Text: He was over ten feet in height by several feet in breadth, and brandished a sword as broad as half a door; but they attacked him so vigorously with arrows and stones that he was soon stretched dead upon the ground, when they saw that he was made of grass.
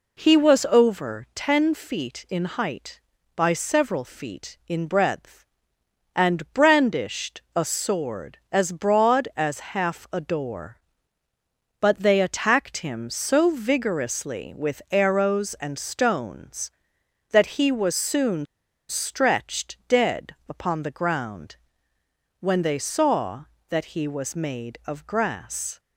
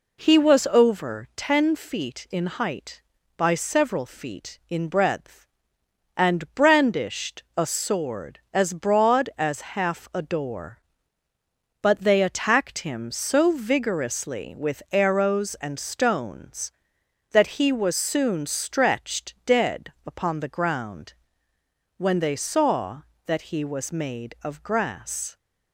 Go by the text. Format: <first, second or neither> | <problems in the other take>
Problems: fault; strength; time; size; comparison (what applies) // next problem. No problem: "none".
second | pauses between "soon" and "stretched"; at 18.4 s; 0.45 s long